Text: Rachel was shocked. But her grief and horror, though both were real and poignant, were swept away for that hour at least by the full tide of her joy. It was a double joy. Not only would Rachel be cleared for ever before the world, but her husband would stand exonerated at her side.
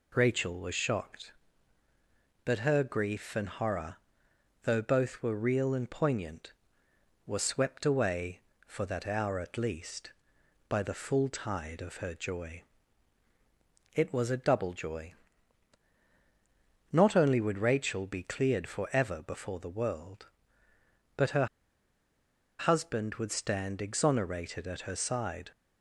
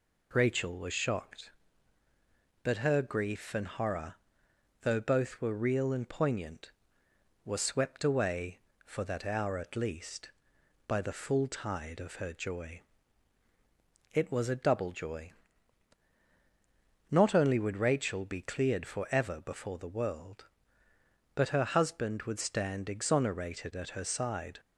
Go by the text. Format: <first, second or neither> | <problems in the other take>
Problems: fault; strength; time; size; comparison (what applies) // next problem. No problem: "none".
second | pauses between "her" and "husband"; at 21.4 s; 1.1 s long